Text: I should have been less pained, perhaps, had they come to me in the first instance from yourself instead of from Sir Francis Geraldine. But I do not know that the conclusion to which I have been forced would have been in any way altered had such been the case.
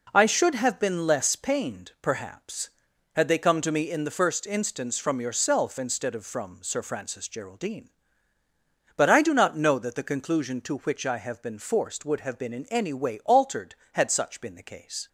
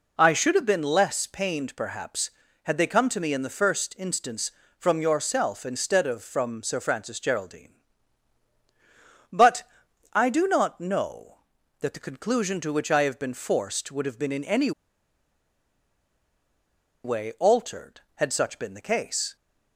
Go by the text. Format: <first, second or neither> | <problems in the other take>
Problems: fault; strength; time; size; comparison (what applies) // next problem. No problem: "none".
first | pauses between "But" and "I"; noticeable; at 9.6 s; 0.50 s long // pauses between "any" and "way"; strong; at 14.7 s; 2.3 s long